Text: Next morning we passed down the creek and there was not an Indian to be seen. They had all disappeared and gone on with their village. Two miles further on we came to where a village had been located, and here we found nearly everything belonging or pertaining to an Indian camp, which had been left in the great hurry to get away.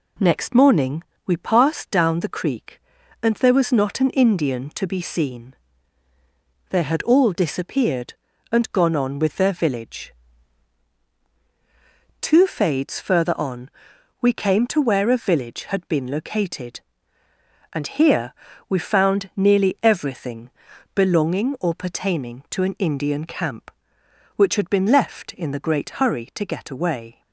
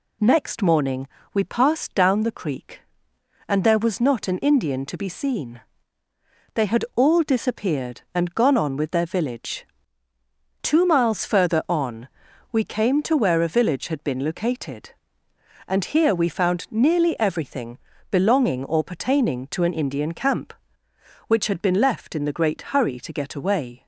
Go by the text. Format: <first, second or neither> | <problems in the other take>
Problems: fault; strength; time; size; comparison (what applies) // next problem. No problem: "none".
second | pauses between "morning" and "we"; slight; at 1.0 s; 0.24 s long; slight in the second // says "fades" for "miles"; at 12.4 s // pauses between "on" and "we"; noticeable; at 13.6 s; 0.50 s long; also in the second // pauses between "here" and "we"; slight; at 18.3 s; 0.34 s long // pauses between "everything" and "belonging"; noticeable; at 20.4 s; 0.46 s long; slight in the second